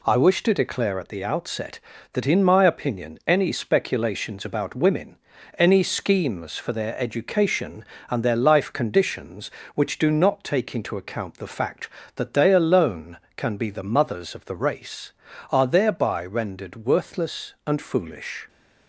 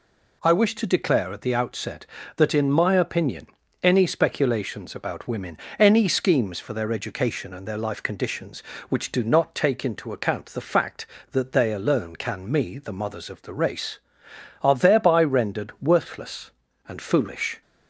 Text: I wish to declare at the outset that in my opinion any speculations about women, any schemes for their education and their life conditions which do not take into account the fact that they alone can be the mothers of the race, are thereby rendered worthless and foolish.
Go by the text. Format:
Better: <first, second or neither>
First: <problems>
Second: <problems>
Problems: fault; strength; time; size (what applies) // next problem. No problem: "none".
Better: first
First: none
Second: pauses between "opinion" and "any"; slight; at 3.4 s; 0.36 s long // says "me" for "be"; at 12.4 s